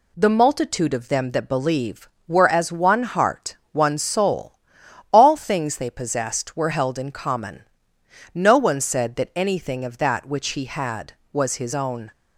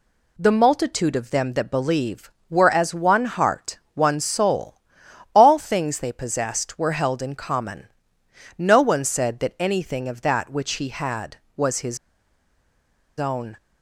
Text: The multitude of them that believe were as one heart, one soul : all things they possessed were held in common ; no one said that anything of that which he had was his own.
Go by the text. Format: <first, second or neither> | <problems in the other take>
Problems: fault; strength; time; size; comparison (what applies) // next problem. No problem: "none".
first | pauses between "his" and "own"; at 11.9 s; 1.2 s long